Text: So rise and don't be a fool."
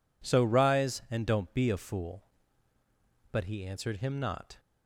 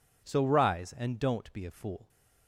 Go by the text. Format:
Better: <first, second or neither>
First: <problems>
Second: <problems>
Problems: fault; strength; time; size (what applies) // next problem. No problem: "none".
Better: second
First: goes on to say "But he answered him not"; noticeable; from 3.3 s on; 1.2 s long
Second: none